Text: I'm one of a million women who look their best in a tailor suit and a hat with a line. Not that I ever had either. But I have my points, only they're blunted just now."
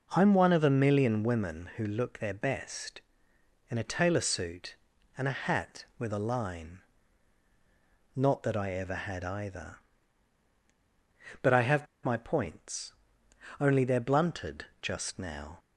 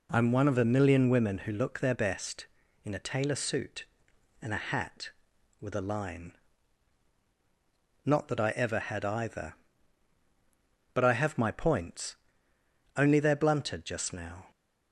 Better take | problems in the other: second | pauses between "have" and "my"; slight; at 11.8 s; 0.18 s long // pauses between "blunted" and "just"; slight; at 14.6 s; 0.16 s long

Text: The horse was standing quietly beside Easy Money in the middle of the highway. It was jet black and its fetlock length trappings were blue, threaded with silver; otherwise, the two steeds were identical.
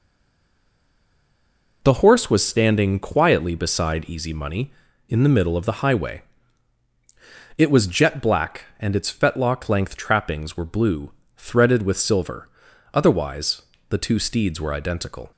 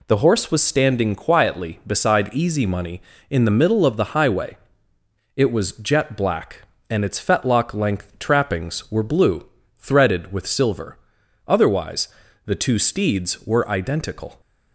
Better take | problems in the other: second | stays silent before the first word; noticeable; until 1.8 s; 1.8 s long

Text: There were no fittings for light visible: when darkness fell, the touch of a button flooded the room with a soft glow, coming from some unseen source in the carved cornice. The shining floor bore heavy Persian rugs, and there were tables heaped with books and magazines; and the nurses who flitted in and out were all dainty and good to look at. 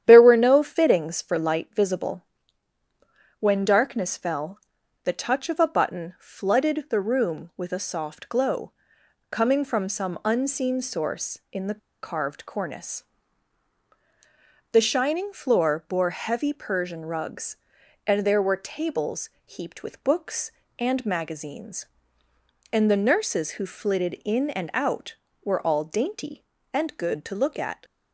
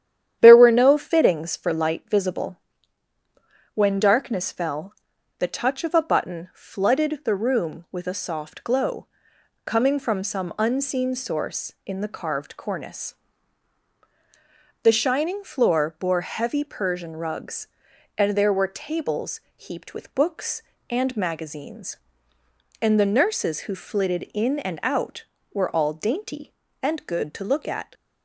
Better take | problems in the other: second | starts louder than the rest; strong; until 1.0 s; 10 dB; strong in the second // pauses between "the" and "carved"; slight; at 11.7 s; 0.23 s long // pauses between "tables" and "heaped"; slight; at 19.2 s; 0.16 s long; slight in the second

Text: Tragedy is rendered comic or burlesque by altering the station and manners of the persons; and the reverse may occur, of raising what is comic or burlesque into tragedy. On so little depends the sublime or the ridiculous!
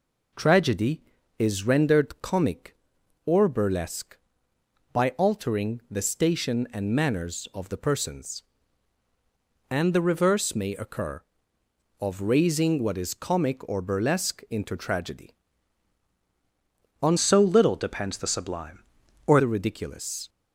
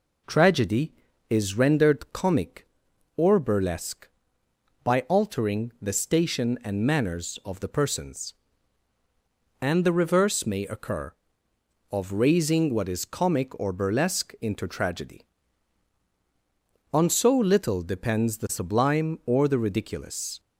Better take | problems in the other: second | changes voice from "so" to "or"; from 17.1 to 19.4 s; 2.3 s long

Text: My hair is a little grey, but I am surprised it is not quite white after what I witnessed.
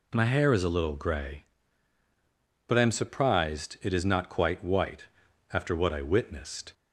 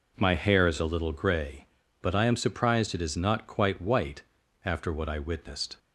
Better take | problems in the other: neither | pauses between "white" and "after"; the same in both

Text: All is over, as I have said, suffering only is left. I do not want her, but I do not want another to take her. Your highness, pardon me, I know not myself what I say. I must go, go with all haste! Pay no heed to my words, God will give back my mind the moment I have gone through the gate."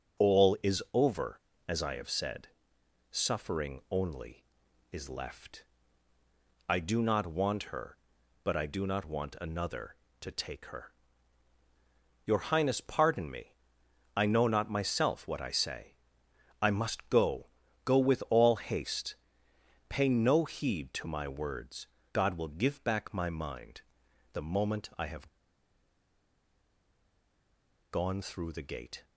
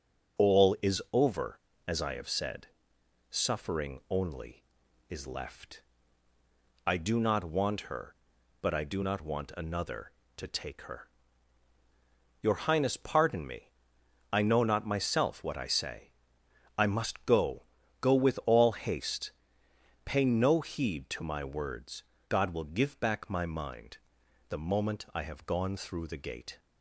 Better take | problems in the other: second | starts louder than the rest; until 1.3 s; 6.5 dB // pauses between "mind" and "the"; noticeable; at 23.8 s; 0.50 s long; noticeable in the second // pauses between "have" and "gone"; strong; at 25.2 s; 2.6 s long

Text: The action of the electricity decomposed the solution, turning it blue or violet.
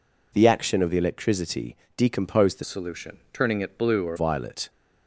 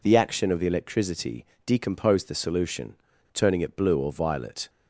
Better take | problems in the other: second | pauses between "electricity" and "decomposed"; slight; at 1.7 s; 0.20 s long; slight in the second // changes voice from "solution" to "or"; from 2.6 to 4.1 s; 1.5 s long

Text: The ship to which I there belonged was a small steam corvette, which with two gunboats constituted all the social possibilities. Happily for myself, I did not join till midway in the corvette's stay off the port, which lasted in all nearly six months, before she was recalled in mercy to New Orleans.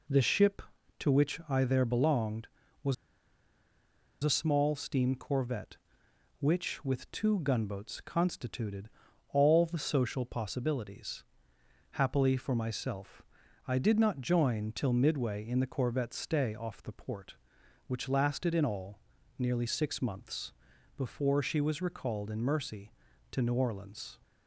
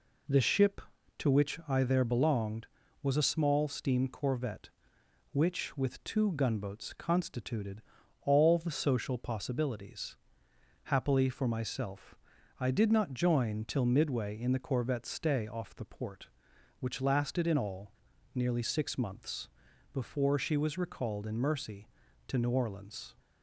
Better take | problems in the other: second | pauses between "was" and "a"; strong; at 2.9 s; 1.2 s long // pauses between "constituted" and "all"; at 8.8 s; 0.42 s long; also in the second // pauses between "all" and "nearly"; at 18.9 s; 0.40 s long; also in the second

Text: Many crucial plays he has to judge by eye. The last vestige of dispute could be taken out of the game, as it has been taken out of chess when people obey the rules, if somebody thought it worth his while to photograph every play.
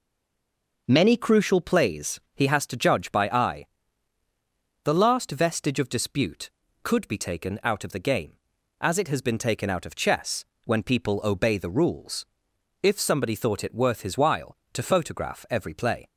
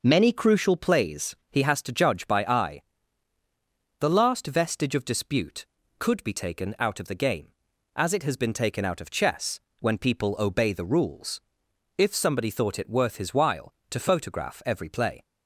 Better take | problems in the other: second | stays silent before the first word; slight; until 0.8 s; 0.8 s long // pauses between "plays" and "he"; slight; at 2.1 s; 0.16 s long; slight in the second // pauses between "chess" and "when"; slight; at 10.4 s; 0.20 s long; slight in the second

